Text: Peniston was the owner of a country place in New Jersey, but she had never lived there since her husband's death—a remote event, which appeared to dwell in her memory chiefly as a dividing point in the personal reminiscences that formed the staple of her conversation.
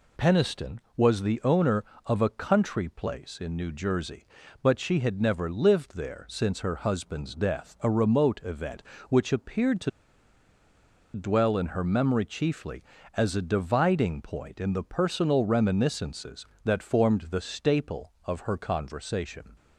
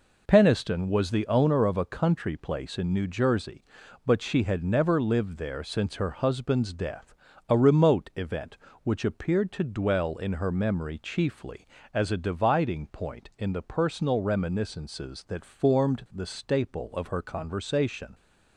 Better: second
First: pauses between "to" and "dwell"; strong; at 9.8 s; 1.2 s long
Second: none

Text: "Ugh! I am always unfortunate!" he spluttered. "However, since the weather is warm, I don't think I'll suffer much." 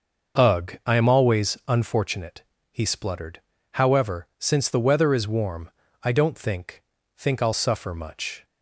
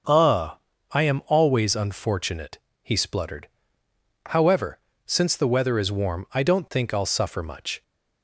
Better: second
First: starts louder than the rest; until 1.4 s; 6 dB // says "think" twice; at 7.1 s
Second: starts louder than the rest; until 1.4 s; 6.5 dB

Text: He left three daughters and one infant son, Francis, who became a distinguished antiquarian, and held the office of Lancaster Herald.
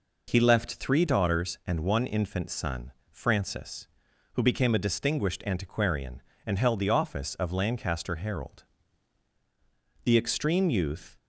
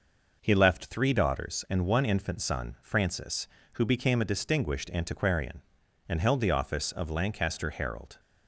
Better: second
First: goes on to say "The extreme youth"; noticeable; from 10.0 s on; 1.1 s long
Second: none

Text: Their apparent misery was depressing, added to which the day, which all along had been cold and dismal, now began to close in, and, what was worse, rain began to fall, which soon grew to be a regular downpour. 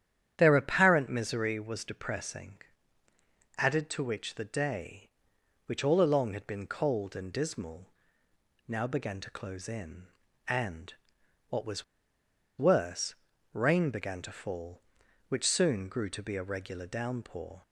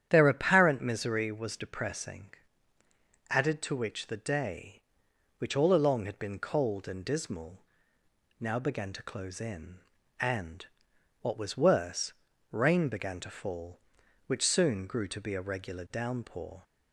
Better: second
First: starts louder than the rest; strong; until 1.3 s; 10 dB // pauses between "was" and "worse"; noticeable; at 11.8 s; 0.74 s long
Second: starts louder than the rest; strong; until 1.1 s; 10 dB

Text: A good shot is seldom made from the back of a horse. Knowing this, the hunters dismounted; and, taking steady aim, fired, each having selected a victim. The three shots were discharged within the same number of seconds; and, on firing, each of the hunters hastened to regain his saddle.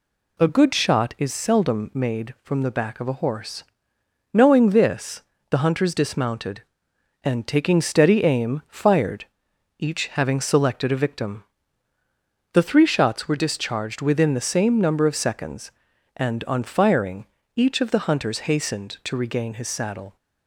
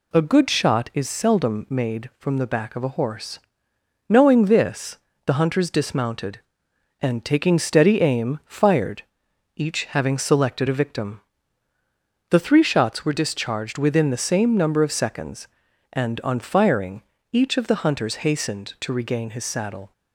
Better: neither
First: none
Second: none

